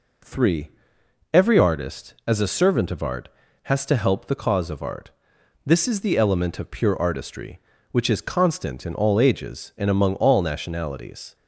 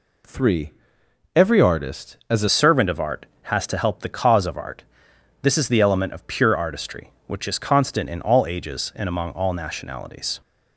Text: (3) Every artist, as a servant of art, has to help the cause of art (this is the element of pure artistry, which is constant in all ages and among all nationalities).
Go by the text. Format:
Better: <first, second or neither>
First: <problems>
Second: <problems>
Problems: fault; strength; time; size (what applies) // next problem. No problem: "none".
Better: first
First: none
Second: changes voice at "servant"; from 2.4 s on; 8.0 s long